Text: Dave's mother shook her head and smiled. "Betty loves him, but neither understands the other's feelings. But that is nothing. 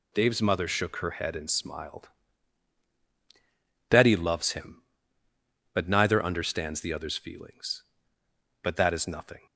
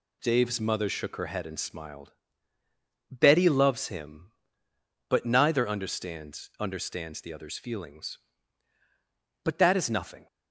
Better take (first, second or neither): first